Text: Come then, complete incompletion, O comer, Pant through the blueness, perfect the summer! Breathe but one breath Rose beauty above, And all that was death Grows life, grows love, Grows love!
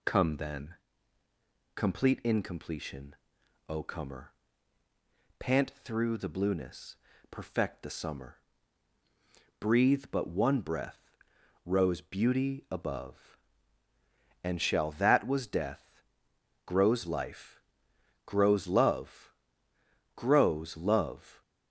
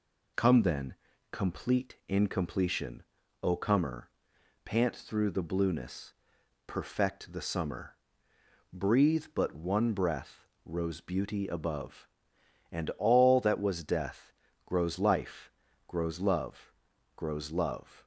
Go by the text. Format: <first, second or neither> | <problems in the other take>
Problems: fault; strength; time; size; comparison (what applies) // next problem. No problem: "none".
second | pauses between "breath" and "Rose"; noticeable; at 10.9 s; 0.64 s long; slight in the second // says "shall" for "all"; at 14.5 s // pauses between "death" and "Grows"; noticeable; at 16.0 s; 0.64 s long; slight in the second